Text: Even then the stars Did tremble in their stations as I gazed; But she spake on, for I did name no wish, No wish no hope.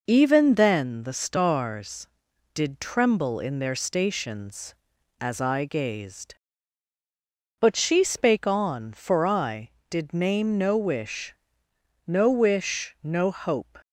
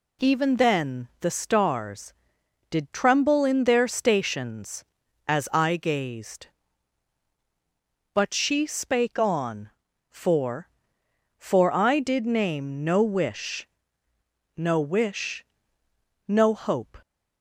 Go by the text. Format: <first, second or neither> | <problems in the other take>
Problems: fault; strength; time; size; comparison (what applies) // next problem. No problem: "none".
first | says "for" twice; at 11.3 s // pauses between "wish" and "no"; noticeable; at 15.4 s; 0.82 s long